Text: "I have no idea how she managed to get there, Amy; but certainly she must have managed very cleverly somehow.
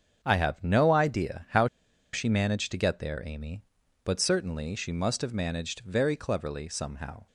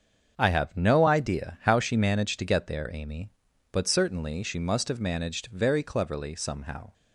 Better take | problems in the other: second | starts louder than the rest; strong; until 1.2 s; 7 dB; also in the second // pauses between "how" and "she"; noticeable; at 1.6 s; 0.47 s long

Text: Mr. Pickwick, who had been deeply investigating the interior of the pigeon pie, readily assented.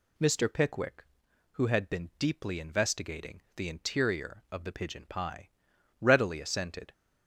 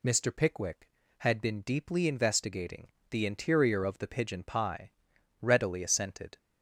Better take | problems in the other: first | skips "who"; at 1.0 s // pauses between "investigating" and "the"; slight; at 2.8 s; 0.24 s long

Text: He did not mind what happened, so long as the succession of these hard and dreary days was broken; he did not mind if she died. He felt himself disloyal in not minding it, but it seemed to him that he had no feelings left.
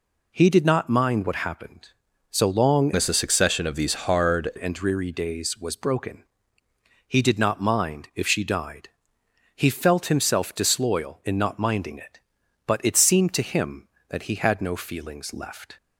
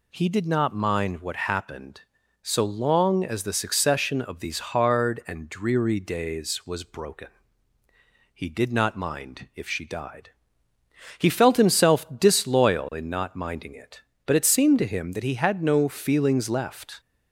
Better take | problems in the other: second | changes voice from "as" to "hard"; from 2.9 to 4.5 s; 1.6 s long

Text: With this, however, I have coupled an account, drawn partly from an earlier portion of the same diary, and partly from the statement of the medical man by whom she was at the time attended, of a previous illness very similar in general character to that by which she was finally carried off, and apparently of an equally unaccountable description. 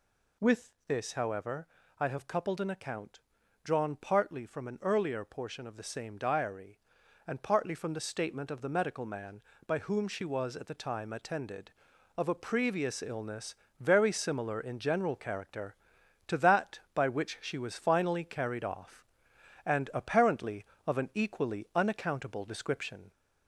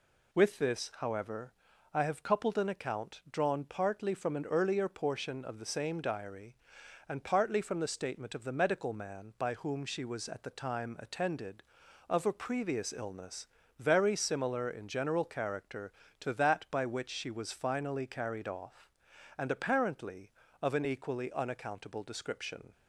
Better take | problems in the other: second | gets louder; slight; throughout; 2.5 dB // pauses between "With" and "this"; slight; at 0.7 s; 0.16 s long // pauses between "illness" and "very"; slight; at 13.5 s; 0.24 s long; slight in the second

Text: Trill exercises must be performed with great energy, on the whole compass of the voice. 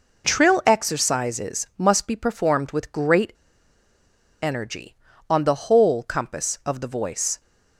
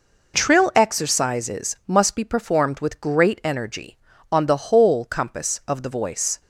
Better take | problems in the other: second | pauses between "great" and "energy"; at 3.3 s; 1.1 s long

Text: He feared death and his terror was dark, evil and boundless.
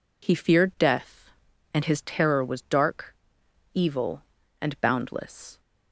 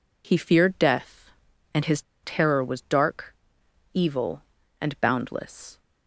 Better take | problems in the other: first | pauses between "his" and "terror"; slight; at 2.0 s; 0.21 s long

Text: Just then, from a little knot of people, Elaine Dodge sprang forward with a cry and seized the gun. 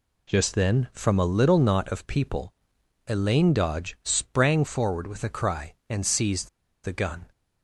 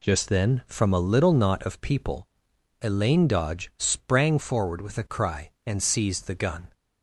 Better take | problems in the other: second | pauses between "seized" and "the"; slight; at 6.4 s; 0.35 s long

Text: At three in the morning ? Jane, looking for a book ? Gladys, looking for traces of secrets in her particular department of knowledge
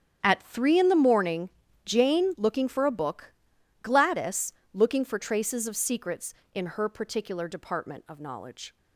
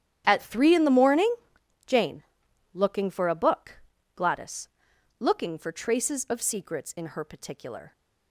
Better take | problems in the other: first | starts louder than the rest; strong; until 1.2 s; 10 dB; strong in the first // stops before "department of knowledge"; at 7.9 s

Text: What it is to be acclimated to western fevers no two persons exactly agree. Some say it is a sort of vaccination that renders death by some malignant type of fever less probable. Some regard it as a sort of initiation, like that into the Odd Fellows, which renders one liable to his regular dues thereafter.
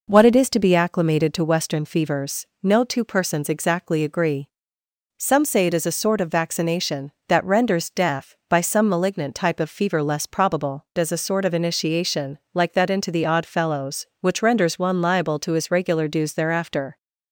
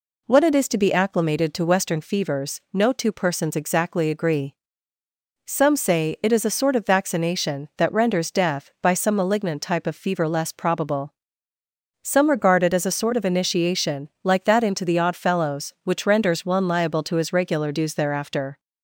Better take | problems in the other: second | pauses between "fevers" and "no"; slight; at 2.4 s; 0.16 s long // skips "Some regard it"; at 10.9 s

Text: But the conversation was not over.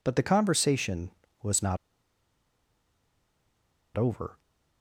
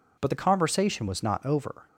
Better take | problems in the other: second | pauses between "not" and "over"; strong; at 1.7 s; 2.1 s long

